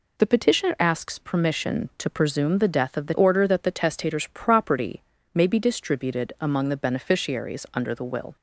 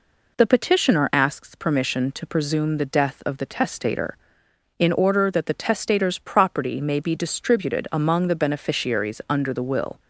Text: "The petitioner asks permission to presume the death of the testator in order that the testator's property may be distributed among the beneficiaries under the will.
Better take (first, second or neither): second